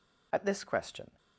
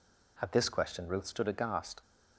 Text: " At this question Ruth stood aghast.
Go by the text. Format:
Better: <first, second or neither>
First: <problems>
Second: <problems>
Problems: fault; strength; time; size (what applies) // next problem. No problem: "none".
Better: second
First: stops before "Ruth stood aghast"; at 1.1 s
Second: none